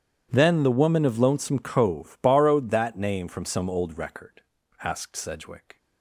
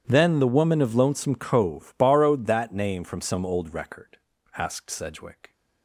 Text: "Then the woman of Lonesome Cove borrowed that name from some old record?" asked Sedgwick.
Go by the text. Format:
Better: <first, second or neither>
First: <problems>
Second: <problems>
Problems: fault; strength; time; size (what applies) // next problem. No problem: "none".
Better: neither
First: starts louder than the rest; strong; until 1.3 s; 10.5 dB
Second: starts louder than the rest; strong; until 1.0 s; 10 dB